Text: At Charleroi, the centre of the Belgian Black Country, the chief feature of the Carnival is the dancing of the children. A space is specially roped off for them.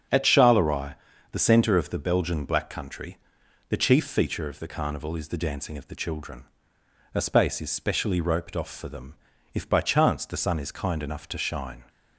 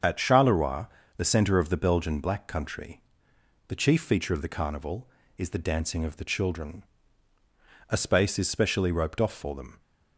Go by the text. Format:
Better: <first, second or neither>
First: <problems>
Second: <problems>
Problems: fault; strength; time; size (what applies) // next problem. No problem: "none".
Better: second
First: starts louder than the rest; strong; until 1.4 s; 7 dB // goes on to say "If by chance the sun is kind enough to shine"; strong; from 9.5 s on; 2.3 s long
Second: starts louder than the rest; until 1.3 s; 7 dB